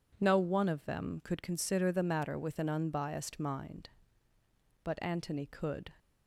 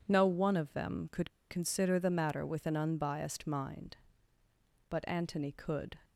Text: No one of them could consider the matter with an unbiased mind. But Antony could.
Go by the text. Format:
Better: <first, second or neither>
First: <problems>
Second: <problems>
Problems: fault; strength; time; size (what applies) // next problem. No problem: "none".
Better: first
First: none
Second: pauses between "could" and "consider"; slight; at 1.2 s; 0.20 s long